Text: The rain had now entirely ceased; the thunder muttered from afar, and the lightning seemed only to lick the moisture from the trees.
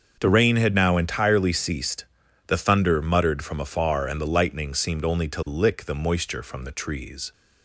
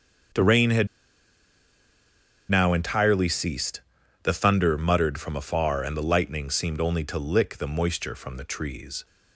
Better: first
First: starts louder than the rest; until 1.2 s; 6.5 dB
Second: starts louder than the rest; until 2.9 s; 6.5 dB // pauses between "had" and "now"; strong; at 0.8 s; 1.6 s long

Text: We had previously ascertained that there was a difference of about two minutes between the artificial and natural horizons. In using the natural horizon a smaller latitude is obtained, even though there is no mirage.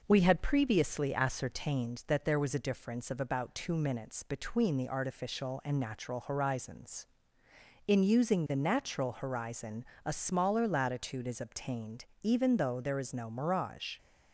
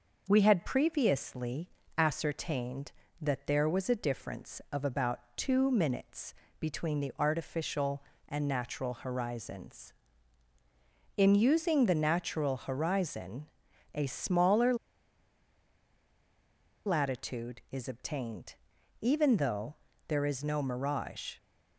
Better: first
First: pauses between "horizon" and "a"; slight; at 9.8 s; 0.22 s long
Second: pauses between "previously" and "ascertained"; slight; at 1.6 s; 0.28 s long // pauses between "about" and "two"; slight; at 5.2 s; 0.16 s long // pauses between "minutes" and "between"; slight; at 6.3 s; 0.24 s long // pauses between "horizon" and "a"; noticeable; at 13.4 s; 0.48 s long // pauses between "smaller" and "latitude"; strong; at 14.7 s; 2.1 s long // pauses between "though" and "there"; slight; at 19.7 s; 0.34 s long

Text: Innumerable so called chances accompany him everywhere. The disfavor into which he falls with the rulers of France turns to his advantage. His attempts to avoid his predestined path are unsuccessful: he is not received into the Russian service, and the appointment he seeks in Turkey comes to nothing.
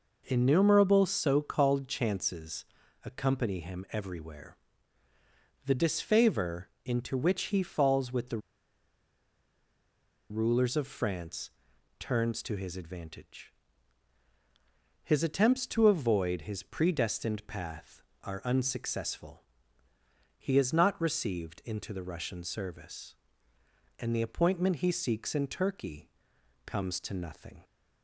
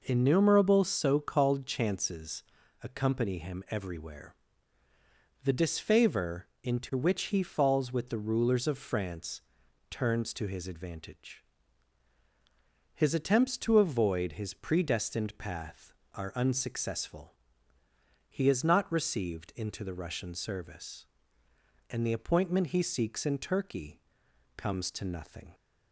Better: second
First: pauses between "chances" and "accompany"; at 2.6 s; 0.40 s long // pauses between "the" and "rulers"; strong; at 8.3 s; 1.9 s long // pauses between "France" and "turns"; noticeable; at 11.4 s; 0.48 s long // pauses between "Turkey" and "comes"; noticeable; at 26.0 s; 0.56 s long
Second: pauses between "chances" and "accompany"; at 2.4 s; 0.40 s long // pauses between "France" and "turns"; noticeable; at 9.4 s; 0.48 s long // pauses between "Turkey" and "comes"; noticeable; at 24.0 s; 0.56 s long

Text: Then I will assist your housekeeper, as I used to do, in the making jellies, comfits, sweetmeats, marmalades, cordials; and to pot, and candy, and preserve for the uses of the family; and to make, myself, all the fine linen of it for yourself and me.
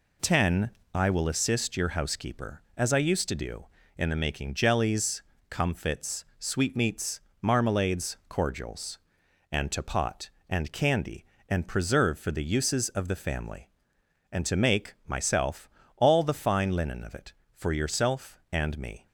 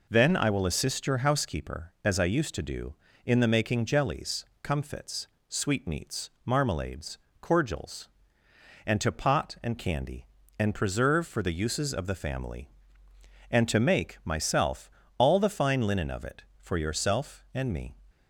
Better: second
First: says "Ten" for "Then"; at 0.2 s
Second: none

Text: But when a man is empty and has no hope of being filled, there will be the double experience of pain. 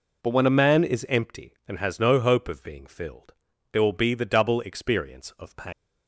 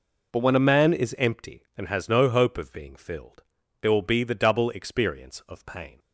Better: second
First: leaves "pain" unfinished; at 5.7 s; 165 ms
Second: none

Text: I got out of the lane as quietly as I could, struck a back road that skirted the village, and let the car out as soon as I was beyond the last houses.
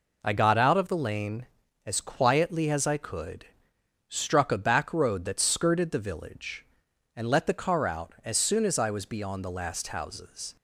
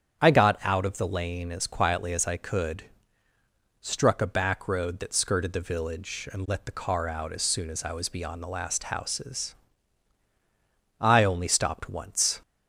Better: first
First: none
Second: starts louder than the rest; strong; until 1.2 s; 8.5 dB // goes on to say "I only stopped once"; from 10.9 s on; 1.4 s long

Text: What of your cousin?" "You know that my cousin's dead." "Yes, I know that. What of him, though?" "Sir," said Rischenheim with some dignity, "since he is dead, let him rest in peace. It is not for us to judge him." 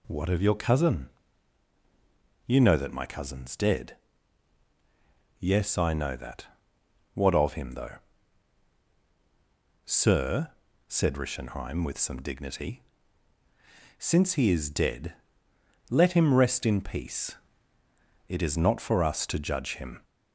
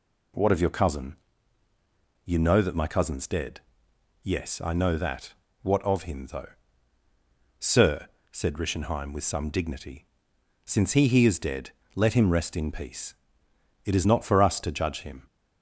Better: first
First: none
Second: says "he" twice; at 11.0 s

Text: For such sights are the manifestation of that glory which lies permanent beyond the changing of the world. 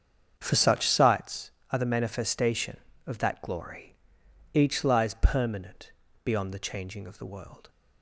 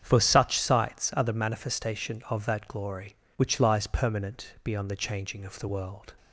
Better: second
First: starts louder than the rest; strong; until 1.3 s; 7.5 dB // says "each" for "which"; at 4.5 s // pauses between "permanent" and "beyond"; slight; at 5.9 s; 0.32 s long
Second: starts louder than the rest; strong; until 1.0 s; 8 dB

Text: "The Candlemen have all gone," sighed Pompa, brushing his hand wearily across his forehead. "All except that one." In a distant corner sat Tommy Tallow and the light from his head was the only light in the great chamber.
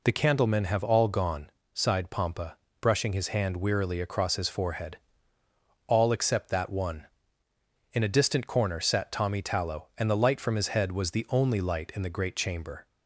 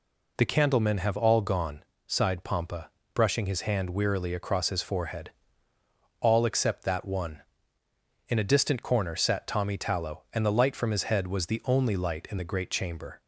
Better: neither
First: none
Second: none

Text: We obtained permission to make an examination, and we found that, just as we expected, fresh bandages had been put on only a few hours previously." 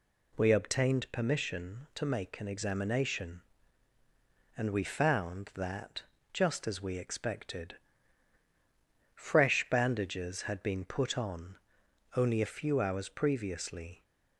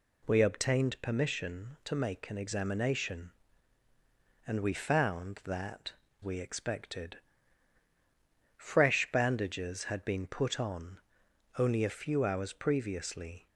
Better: first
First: pauses between "on" and "only"; noticeable; at 11.5 s; 0.60 s long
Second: skips "just as"; at 6.0 s // pauses between "on" and "only"; noticeable; at 10.9 s; 0.60 s long

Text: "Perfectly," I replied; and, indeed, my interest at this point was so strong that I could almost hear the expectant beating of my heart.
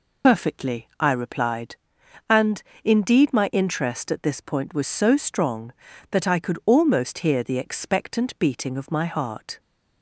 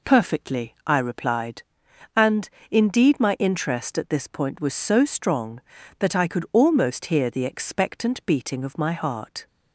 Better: second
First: loses the start of "Perfectly"; at 0.2 s; 80 ms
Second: none

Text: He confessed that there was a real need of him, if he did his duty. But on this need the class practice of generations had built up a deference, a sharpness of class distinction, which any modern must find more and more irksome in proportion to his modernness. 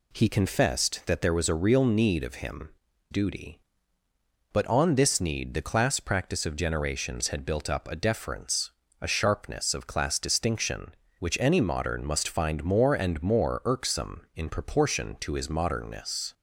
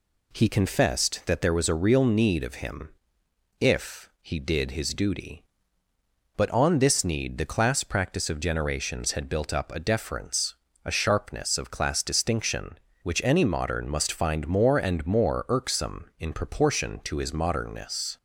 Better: second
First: skips "if he did his"; at 2.9 s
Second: none

